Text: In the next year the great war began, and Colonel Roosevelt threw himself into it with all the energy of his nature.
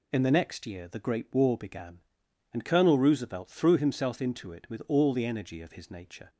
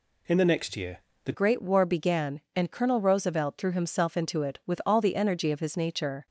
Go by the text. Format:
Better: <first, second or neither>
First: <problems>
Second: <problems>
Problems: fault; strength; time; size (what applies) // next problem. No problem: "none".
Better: first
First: none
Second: pauses between "year" and "the"; slight; at 0.9 s; 0.26 s long // changes voice at "great"; from 1.3 s on; 4.9 s long